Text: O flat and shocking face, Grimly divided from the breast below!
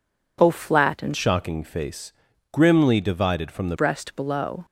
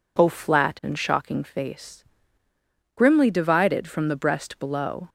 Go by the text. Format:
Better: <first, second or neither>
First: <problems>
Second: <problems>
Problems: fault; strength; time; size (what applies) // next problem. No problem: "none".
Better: second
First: changes voice from "shocking" to "the"; from 1.1 to 3.7 s; 2.6 s long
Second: none